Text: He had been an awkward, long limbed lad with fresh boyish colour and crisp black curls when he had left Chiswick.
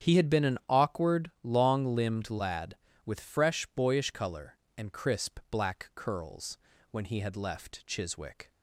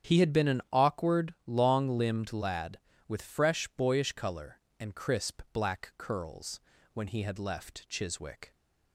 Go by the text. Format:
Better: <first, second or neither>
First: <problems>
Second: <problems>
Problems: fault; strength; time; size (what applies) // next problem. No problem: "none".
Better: neither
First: starts louder than the rest; strong; until 1.1 s; 8.5 dB // pauses between "curls" and "when"; slight; at 6.5 s; 0.32 s long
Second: starts louder than the rest; strong; until 1.1 s; 9 dB // pauses between "curls" and "when"; slight; at 6.5 s; 0.32 s long